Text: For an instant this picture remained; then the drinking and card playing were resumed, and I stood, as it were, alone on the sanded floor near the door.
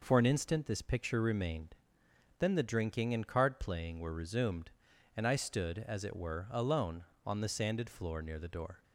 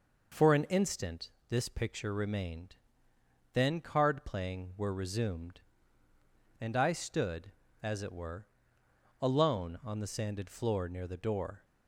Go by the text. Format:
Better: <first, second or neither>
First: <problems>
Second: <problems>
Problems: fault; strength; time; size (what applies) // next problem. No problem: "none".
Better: first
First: none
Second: pauses between "instant" and "this"; slight; at 1.2 s; 0.22 s long // skips "the drinking and"; at 3.8 s